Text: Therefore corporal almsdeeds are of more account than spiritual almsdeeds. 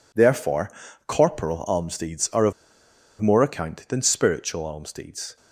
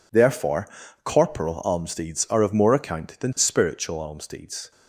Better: second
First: pauses between "Therefore" and "corporal"; slight; at 0.7 s; 0.36 s long // pauses between "of" and "more"; noticeable; at 2.5 s; 0.68 s long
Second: pauses between "Therefore" and "corporal"; slight; at 0.6 s; 0.36 s long

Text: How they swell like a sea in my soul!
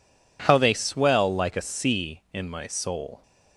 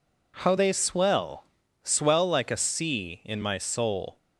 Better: first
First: none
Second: says "swell" twice; at 1.8 s

